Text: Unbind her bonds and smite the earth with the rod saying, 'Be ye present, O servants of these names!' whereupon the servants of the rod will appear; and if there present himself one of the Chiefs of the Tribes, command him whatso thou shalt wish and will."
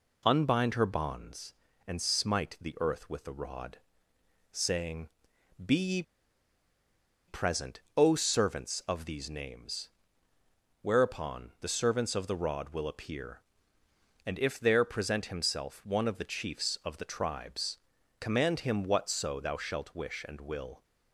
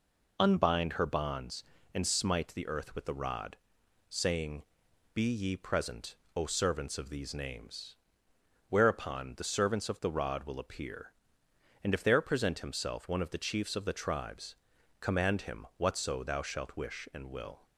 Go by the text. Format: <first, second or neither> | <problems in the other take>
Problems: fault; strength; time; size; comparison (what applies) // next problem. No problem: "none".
second | pauses between "rod" and "saying"; noticeable; at 3.7 s; 0.74 s long; noticeable in the second // pauses between "ye" and "present"; strong; at 6.0 s; 1.2 s long